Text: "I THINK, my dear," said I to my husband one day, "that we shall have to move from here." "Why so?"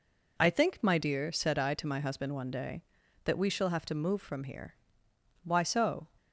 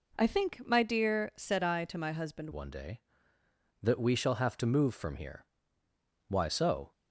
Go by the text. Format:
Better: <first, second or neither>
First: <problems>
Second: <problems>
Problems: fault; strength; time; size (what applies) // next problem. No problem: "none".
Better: first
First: none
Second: changes voice at "one"; from 2.5 s on; 4.4 s long